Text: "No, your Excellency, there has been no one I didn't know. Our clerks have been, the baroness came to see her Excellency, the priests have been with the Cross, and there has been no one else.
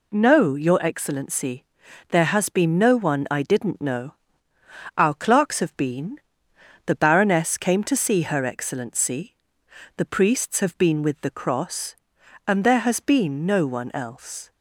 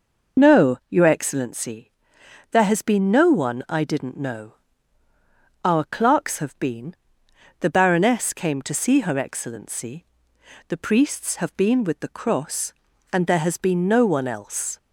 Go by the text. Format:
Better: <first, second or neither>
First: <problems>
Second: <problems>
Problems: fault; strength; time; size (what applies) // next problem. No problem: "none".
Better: first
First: none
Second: loses the start of "No"; at 0.3 s; 30 ms